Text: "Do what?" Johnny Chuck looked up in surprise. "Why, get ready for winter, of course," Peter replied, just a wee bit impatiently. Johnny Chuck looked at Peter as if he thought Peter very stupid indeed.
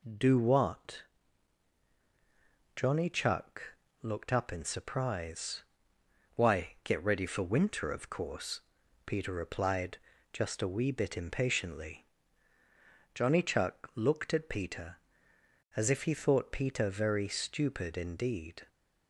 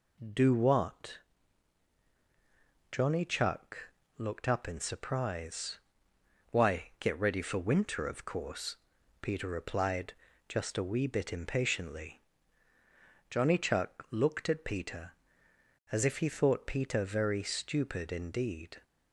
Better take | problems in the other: neither | pauses between "Chuck" and "looked"; slight; the same in both

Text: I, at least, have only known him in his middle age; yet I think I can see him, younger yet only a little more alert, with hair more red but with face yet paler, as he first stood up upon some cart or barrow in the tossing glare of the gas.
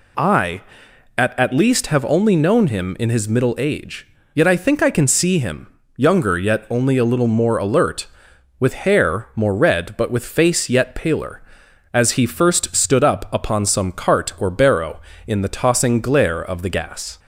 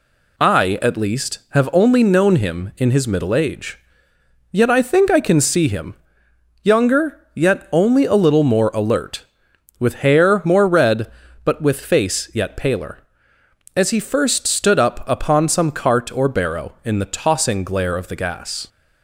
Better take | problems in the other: second | says "at" twice; at 1.3 s

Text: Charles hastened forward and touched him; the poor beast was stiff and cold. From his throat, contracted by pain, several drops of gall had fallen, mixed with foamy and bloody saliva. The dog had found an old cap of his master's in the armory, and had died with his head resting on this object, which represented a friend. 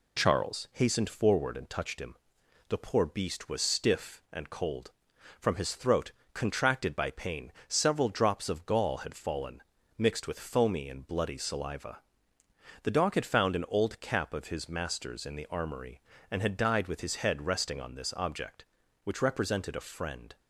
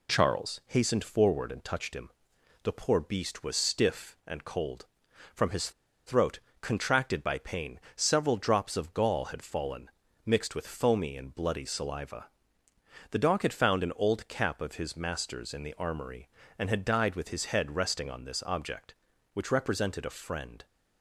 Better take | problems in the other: first | pauses between "his" and "throat"; slight; at 5.7 s; 0.36 s long

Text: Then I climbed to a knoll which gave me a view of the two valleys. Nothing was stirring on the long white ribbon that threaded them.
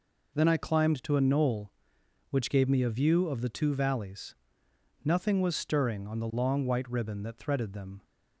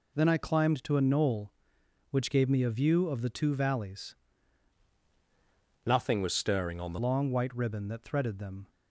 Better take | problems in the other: first | changes voice from "Nothing" to "the"; from 5.8 to 6.9 s; 1.1 s long

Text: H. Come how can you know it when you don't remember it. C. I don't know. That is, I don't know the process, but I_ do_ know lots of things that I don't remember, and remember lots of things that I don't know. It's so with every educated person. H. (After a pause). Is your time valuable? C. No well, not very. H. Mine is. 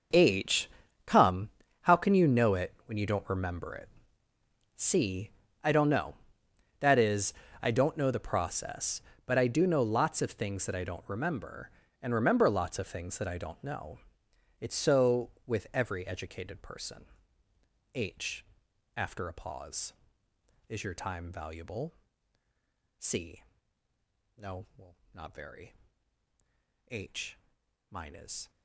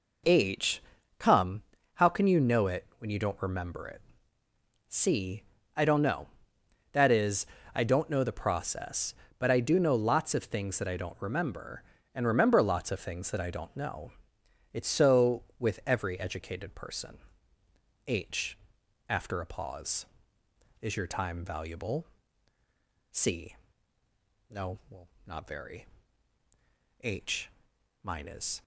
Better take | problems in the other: second | gets quieter; strong; throughout; 16 dB // pauses between "Come" and "how"; slight; at 1.4 s; 0.36 s long; slight in the second

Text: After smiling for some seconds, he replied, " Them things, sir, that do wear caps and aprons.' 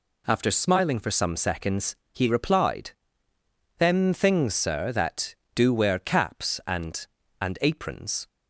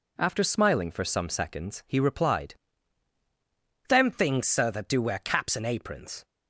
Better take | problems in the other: second | says "and" twice; at 7.4 s

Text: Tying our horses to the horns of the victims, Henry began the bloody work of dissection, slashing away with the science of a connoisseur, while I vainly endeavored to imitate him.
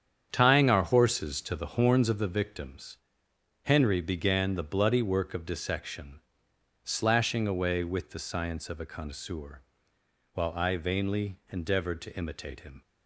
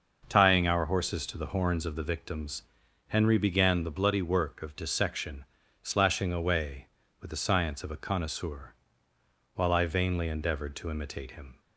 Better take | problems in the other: second | gets quieter; strong; throughout; 9.5 dB // starts louder than the rest; strong; until 1.3 s; 8.5 dB; noticeable in the second

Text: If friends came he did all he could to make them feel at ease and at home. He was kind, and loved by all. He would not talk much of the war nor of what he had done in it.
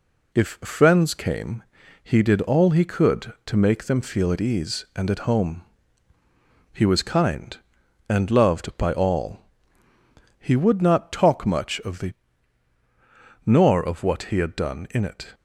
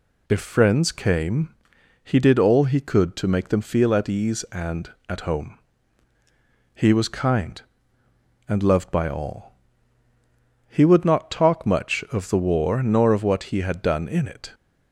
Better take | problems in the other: second | pauses between "came" and "he"; at 1.6 s; 0.40 s long; noticeable in the second // skips "war"; at 12.7 s

